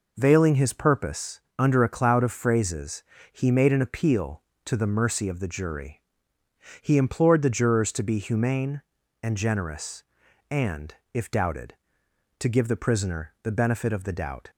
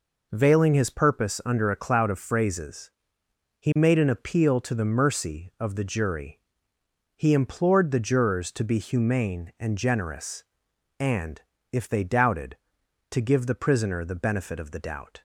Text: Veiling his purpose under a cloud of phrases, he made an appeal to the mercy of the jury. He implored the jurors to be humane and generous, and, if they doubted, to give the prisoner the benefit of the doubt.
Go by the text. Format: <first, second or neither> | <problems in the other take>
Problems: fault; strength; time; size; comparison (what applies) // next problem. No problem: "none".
second | pauses between "purpose" and "under"; slight; at 1.3 s; 0.18 s long // skips "they"; at 11.3 s